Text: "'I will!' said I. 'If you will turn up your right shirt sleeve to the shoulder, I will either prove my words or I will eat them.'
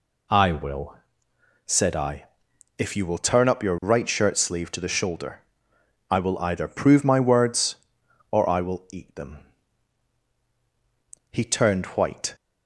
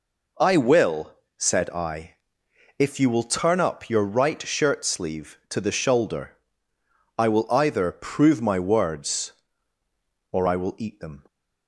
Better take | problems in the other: second | goes on to say "He turned white"; noticeable; from 11.3 s on; 1.0 s long

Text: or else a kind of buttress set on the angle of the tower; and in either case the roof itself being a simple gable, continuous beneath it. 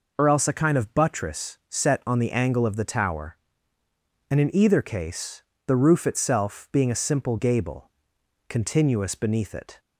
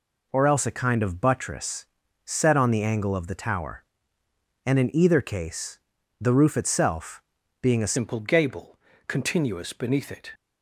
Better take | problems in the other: first | pauses between "buttress" and "set"; at 1.8 s; 0.40 s long // pauses between "case" and "the"; at 5.7 s; 0.42 s long; slight in the first // pauses between "itself" and "being"; at 7.2 s; 0.38 s long // changes voice at "simple"; from 7.9 s on; 2.4 s long

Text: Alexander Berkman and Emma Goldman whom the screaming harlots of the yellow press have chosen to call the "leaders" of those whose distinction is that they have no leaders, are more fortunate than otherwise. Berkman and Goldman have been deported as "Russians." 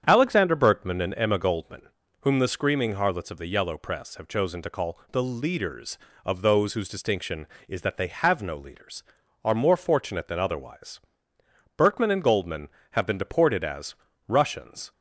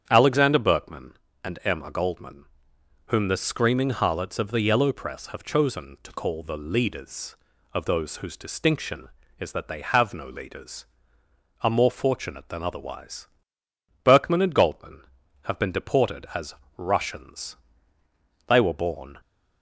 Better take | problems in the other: first | starts louder than the rest; strong; until 1.1 s; 9 dB; strong in the first // pauses between "Goldman" and "whom"; noticeable; at 2.4 s; 0.64 s long; slight in the first // pauses between "as" and "Russians"; slight; at 16.5 s; 0.26 s long; slight in the first // goes on to say "They were born"; noticeable; from 18.4 s on; 0.70 s long

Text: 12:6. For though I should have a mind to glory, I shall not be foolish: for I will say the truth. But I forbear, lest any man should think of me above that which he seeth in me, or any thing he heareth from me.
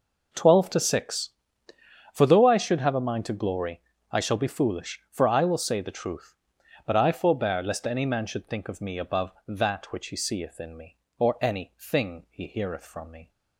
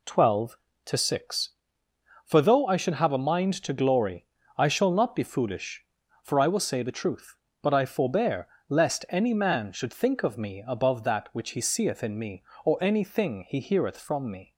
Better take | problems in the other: second | skips "not"; at 4.3 s

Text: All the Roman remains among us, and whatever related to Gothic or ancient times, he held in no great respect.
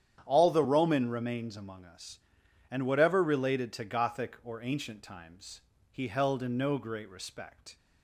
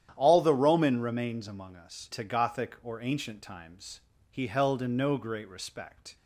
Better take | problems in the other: first | starts louder than the rest; strong; until 1.1 s; 10.5 dB; strong in the first // skips "and whatever related"; at 2.1 s

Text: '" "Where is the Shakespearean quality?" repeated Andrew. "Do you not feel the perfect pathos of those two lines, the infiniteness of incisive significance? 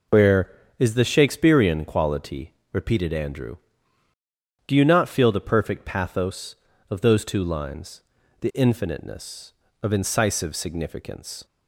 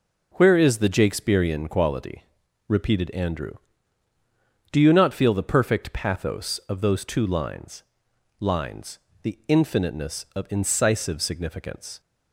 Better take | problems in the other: first | says "lines" twice; at 8.3 s

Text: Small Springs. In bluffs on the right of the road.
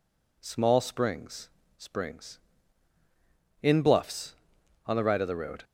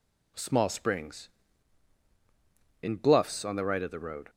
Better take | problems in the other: second | says "Springs" twice; at 1.7 s

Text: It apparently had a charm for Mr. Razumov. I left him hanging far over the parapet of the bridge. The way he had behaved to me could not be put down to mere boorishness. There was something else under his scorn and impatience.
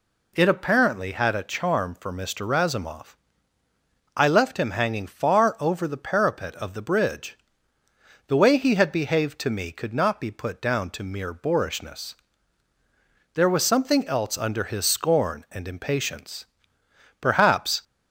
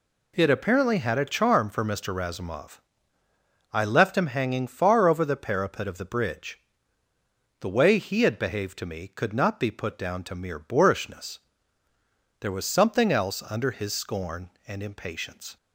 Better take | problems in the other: second | goes on to say "Perhaps"; noticeable; from 17.2 s on; 0.62 s long

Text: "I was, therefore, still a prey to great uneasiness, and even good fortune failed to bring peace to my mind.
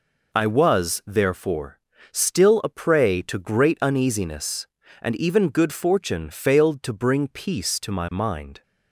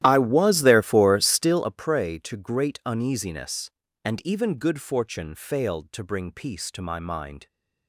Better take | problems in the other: first | starts louder than the rest; strong; until 1.7 s; 13 dB

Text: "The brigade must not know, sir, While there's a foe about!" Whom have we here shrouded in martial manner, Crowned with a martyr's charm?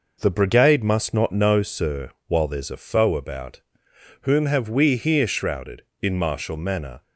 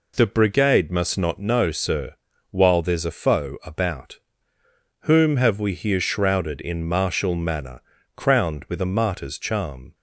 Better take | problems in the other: second | stops before "Crowned with a martyr's charm"; at 7.0 s

